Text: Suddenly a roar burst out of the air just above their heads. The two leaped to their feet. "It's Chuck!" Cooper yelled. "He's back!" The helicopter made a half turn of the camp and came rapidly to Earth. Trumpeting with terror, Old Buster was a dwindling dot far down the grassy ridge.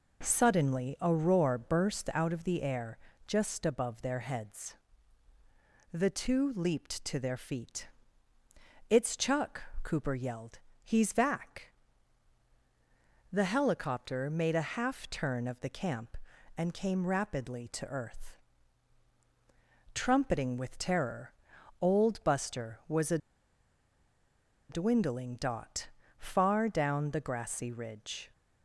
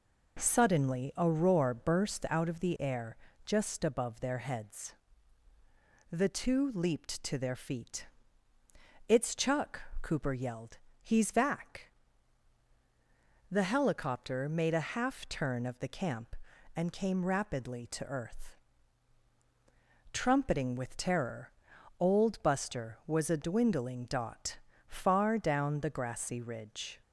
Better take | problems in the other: second | pauses between "air" and "just"; slight; at 2.9 s; 0.28 s long; slight in the second // pauses between "a" and "dwindling"; strong; at 23.1 s; 1.5 s long // pauses between "dot" and "far"; slight; at 25.8 s; 0.32 s long; slight in the second

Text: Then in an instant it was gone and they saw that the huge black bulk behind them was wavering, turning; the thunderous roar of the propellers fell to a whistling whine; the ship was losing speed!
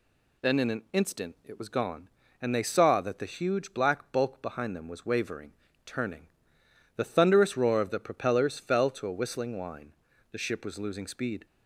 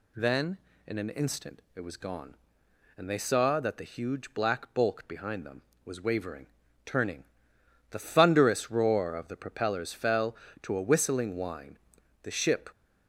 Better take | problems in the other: first | stops before "was losing speed"; at 12.7 s

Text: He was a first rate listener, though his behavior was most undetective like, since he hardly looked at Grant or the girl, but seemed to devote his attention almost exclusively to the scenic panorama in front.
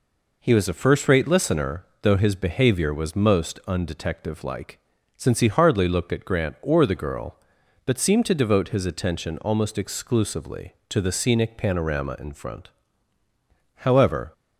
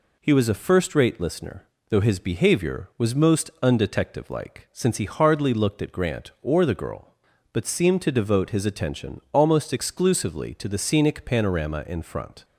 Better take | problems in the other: second | goes on to say "However"; from 13.7 s on; 0.58 s long

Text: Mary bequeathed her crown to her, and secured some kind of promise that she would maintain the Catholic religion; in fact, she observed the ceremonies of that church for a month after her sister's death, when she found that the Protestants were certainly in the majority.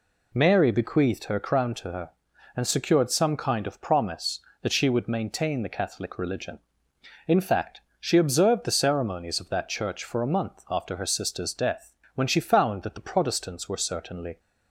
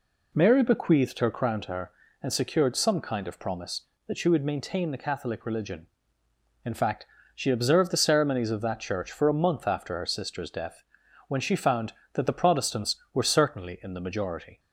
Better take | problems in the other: second | stops before "in the majority"; at 14.3 s

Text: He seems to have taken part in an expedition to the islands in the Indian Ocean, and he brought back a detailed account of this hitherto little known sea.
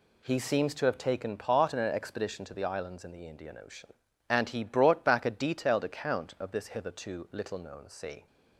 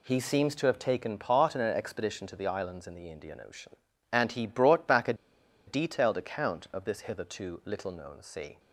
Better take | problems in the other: first | pauses between "a" and "detailed"; noticeable; at 5.1 s; 0.52 s long

